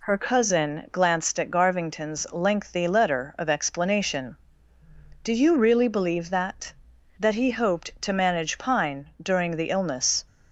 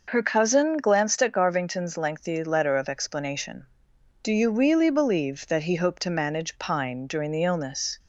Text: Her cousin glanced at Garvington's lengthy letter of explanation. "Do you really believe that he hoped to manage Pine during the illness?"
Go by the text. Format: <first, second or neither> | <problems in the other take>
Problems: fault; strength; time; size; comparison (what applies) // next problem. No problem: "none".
second | says "that" twice; at 7.1 s